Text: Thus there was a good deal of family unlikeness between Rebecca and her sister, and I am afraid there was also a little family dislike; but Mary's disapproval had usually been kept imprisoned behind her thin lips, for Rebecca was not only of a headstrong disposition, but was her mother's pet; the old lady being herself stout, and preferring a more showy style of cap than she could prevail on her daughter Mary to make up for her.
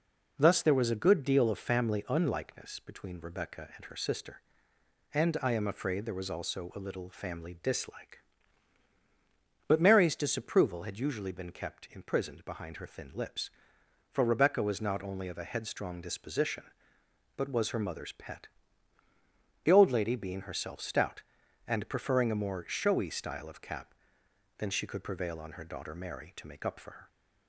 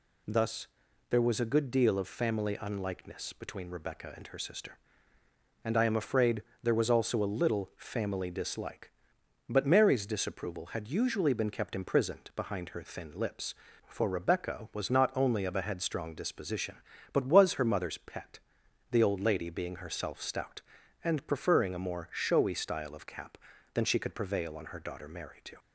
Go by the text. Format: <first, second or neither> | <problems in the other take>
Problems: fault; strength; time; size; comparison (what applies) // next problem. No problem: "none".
first | pauses between "Thus" and "there"; at 0.6 s; 0.44 s long // pauses between "afraid" and "there"; slight; at 6.4 s; 0.20 s long // stops before "make up for her"; at 25.5 s